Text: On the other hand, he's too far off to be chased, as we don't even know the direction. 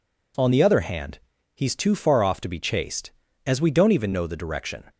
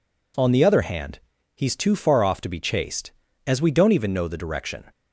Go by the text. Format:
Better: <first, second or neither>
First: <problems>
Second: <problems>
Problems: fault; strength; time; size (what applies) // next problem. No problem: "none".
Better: neither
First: none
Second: none